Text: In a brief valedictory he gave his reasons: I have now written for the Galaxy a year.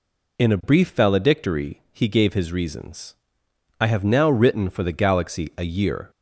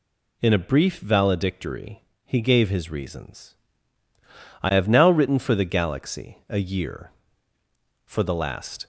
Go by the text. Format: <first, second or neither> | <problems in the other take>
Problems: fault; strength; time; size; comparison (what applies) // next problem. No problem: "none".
first | pauses between "valedictory" and "he"; slight; at 2.0 s; 0.24 s long // goes on to say "For the last"; noticeable; from 8.0 s on; 0.80 s long